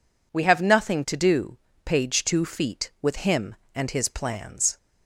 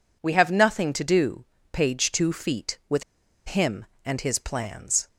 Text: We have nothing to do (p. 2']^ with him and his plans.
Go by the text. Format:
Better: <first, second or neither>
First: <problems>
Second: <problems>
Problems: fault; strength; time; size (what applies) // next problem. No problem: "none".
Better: first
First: none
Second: pauses between "with" and "him"; noticeable; at 3.0 s; 0.54 s long